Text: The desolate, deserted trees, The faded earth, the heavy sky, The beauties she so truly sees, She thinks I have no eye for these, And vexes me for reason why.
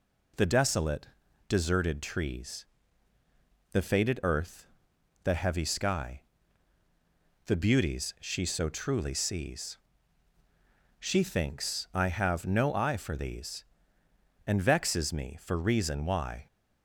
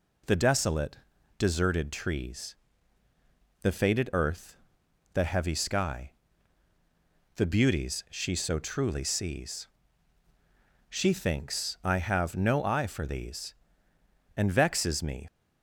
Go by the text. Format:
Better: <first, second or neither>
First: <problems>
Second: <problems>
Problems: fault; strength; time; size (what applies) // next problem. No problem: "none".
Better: first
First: none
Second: stops before "for reason why"; at 15.2 s